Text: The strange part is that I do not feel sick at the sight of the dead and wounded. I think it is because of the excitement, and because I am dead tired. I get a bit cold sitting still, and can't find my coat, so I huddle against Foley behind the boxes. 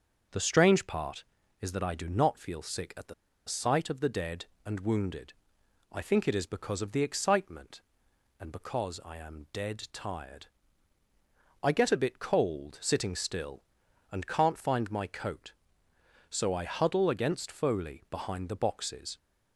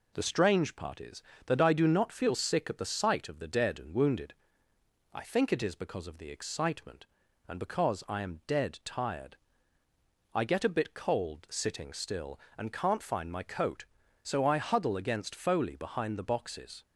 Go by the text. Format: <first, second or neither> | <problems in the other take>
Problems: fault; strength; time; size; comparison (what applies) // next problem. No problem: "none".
second | starts louder than the rest; until 1.6 s; 6.5 dB // pauses between "the" and "sight"; slight; at 3.1 s; 0.33 s long